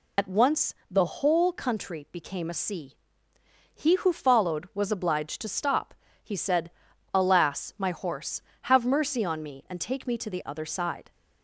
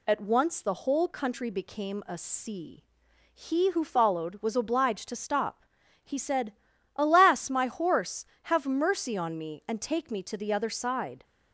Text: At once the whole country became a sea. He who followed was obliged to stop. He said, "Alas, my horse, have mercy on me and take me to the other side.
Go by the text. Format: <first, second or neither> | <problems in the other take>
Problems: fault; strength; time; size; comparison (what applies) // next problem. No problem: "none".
second | loses the start of "At"; at 0.1 s; 50 ms // pauses between "once" and "the"; slight; at 0.7 s; 0.16 s long